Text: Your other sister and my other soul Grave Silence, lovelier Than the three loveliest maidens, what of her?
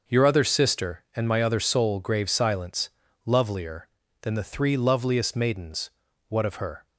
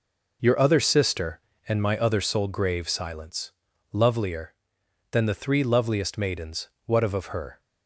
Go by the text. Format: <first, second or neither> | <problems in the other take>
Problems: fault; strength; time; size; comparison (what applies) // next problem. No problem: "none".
first | says "of" twice; at 7.1 s